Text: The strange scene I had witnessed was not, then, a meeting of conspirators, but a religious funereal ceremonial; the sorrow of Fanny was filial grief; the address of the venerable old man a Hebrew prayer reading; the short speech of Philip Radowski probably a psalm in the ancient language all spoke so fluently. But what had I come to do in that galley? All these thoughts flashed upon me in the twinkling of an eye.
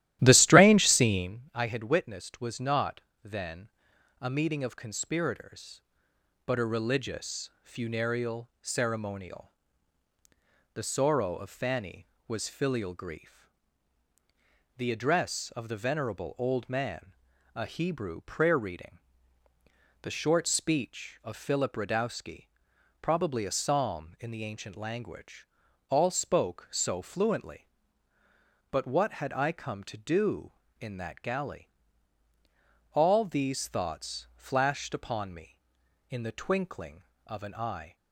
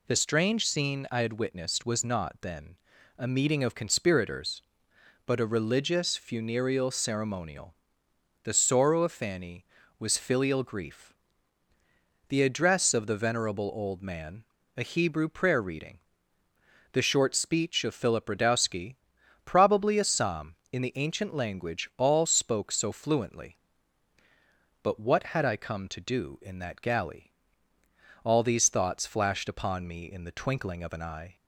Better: second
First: starts louder than the rest; strong; until 1.4 s; 13.5 dB // pauses between "man" and "a"; at 17.1 s; 0.42 s long // pauses between "Radowski" and "probably"; noticeable; at 22.4 s; 0.52 s long // pauses between "language" and "all"; at 25.4 s; 0.40 s long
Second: pauses between "man" and "a"; slight; at 14.4 s; 0.34 s long // pauses between "Radowski" and "probably"; noticeable; at 18.9 s; 0.46 s long

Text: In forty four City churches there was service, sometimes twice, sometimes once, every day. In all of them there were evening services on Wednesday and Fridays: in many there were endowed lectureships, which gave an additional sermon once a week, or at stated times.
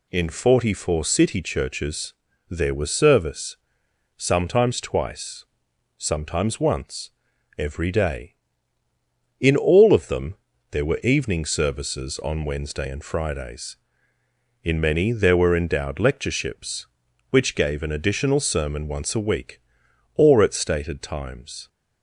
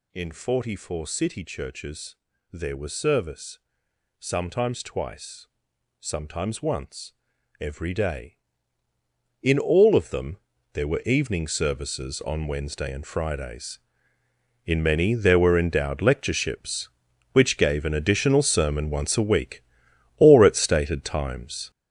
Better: first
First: pauses between "churches" and "there"; slight; at 2.1 s; 0.36 s long // pauses between "them" and "there"; slight; at 10.3 s; 0.34 s long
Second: gets louder; strong; throughout; 9 dB // pauses between "churches" and "there"; slight; at 2.1 s; 0.36 s long // pauses between "them" and "there"; slight; at 10.3 s; 0.34 s long

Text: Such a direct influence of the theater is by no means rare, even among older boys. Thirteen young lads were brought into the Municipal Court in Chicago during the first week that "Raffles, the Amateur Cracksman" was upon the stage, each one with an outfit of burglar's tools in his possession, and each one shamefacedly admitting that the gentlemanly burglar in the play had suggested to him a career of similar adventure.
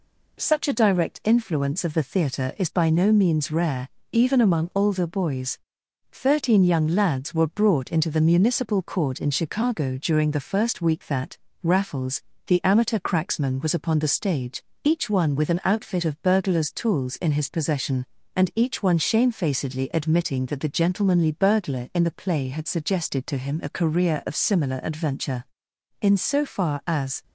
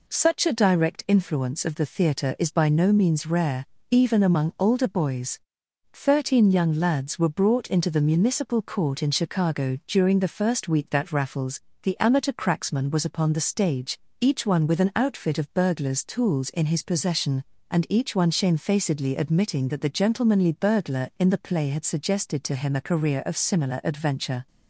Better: second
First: pauses between "that" and "Raffles"; slight; at 11.3 s; 0.24 s long // goes on to say "In so far as"; noticeable; from 26.0 s on; 1.2 s long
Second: none

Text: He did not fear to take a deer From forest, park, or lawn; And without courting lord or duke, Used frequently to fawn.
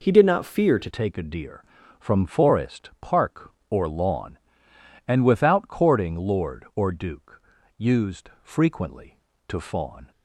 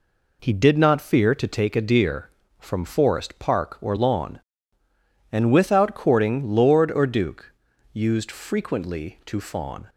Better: second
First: changes voice at "take"; from 0.8 s on; 9.3 s long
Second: none

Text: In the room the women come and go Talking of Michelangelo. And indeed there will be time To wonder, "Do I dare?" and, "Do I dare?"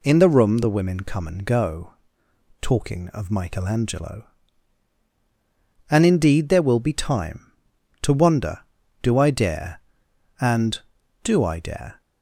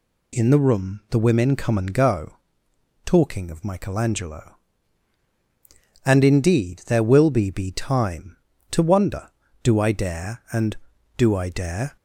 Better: first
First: pauses between "go" and "Talking"; noticeable; at 1.9 s; 0.68 s long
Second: pauses between "go" and "Talking"; noticeable; at 2.3 s; 0.68 s long // says "be" twice; at 7.5 s

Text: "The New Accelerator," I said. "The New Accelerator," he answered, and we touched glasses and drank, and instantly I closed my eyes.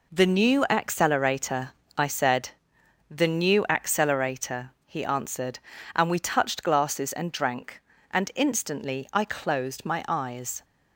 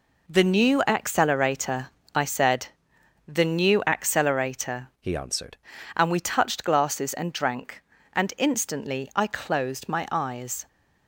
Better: first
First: none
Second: changes voice from "he" to "answered"; from 4.9 to 5.5 s; 0.6 s long

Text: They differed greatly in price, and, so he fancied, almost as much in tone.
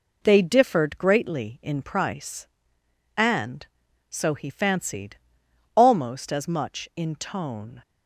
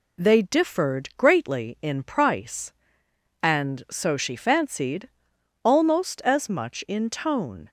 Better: first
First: none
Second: says "she" for "he"; at 4.1 s

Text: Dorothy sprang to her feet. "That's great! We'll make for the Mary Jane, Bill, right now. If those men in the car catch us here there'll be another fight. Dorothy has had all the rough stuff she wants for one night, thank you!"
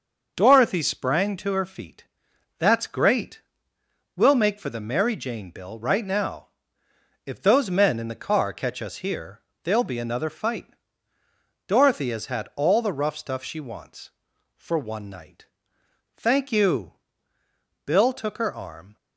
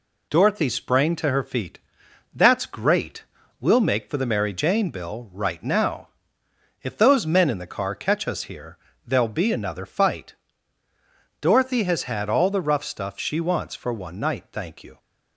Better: second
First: starts louder than the rest; until 1.3 s; 6 dB // pauses between "here" and "there'll"; slight; at 9.4 s; 0.22 s long // goes on to say "Bill took her arm"; noticeable; from 17.8 s on; 1.1 s long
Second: pauses between "here" and "there'll"; slight; at 8.7 s; 0.28 s long

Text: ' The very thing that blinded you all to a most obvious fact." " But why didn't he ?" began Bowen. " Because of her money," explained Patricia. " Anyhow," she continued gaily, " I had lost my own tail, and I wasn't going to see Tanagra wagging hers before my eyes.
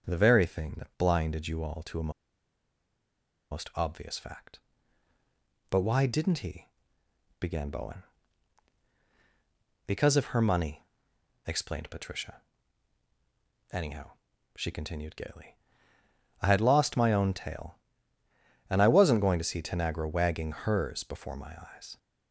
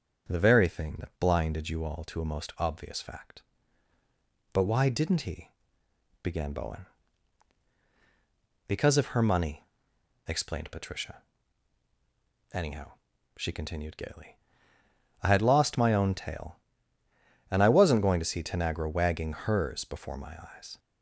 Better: second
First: starts louder than the rest; strong; until 1.0 s; 7 dB // pauses between "a" and "most"; strong; at 2.1 s; 1.4 s long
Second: starts louder than the rest; strong; until 1.3 s; 7.5 dB

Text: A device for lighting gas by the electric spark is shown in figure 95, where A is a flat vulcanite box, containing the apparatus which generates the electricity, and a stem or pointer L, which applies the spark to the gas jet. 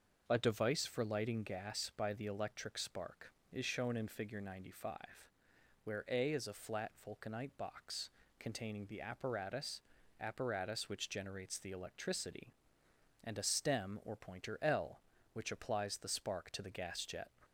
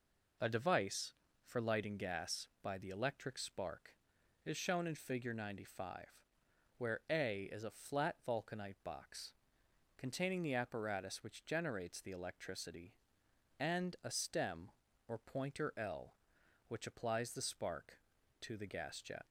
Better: second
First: starts louder than the rest; noticeable; until 1.2 s; 6 dB // pauses between "flat" and "vulcanite"; slight; at 6.8 s; 0.16 s long // says "apparatus" twice; at 10.1 s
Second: none

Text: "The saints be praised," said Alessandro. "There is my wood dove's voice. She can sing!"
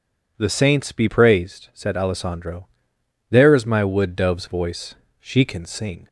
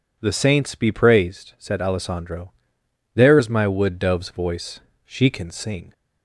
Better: neither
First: none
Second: none

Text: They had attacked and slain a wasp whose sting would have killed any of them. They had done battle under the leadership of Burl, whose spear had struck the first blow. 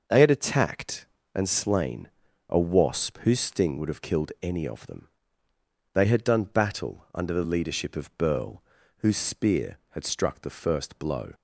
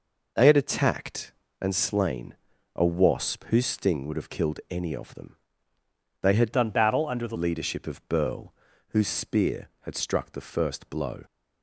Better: first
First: pauses between "slain" and "a"; at 2.0 s; 0.40 s long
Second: pauses between "slain" and "a"; at 2.3 s; 0.40 s long // changes voice from "done" to "the"; from 6.5 to 7.3 s; 0.8 s long

